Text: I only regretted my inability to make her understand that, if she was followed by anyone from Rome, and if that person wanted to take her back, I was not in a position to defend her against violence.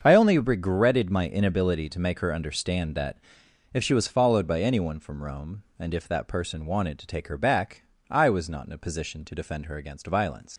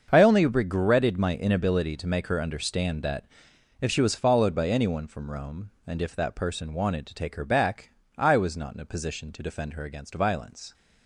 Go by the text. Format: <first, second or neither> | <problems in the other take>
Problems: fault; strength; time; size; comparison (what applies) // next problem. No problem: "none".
second | starts louder than the rest; until 1.0 s; 7 dB; also in the second // leaves "violence" unfinished; at 10.5 s; 95 ms